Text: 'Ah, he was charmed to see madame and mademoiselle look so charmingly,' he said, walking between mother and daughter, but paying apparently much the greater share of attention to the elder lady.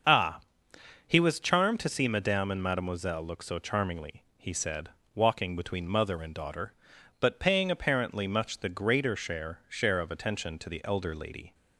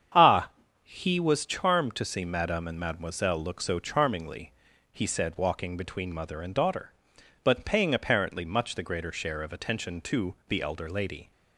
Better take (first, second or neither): second